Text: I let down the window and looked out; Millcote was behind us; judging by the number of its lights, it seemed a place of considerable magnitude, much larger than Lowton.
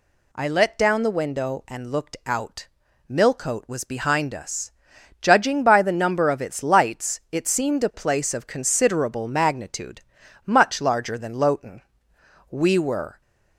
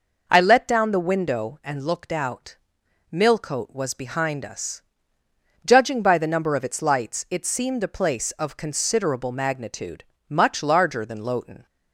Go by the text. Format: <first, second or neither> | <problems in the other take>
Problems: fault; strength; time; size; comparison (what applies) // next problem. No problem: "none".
second | goes on to say "We were"; noticeable; from 12.5 s on; 0.70 s long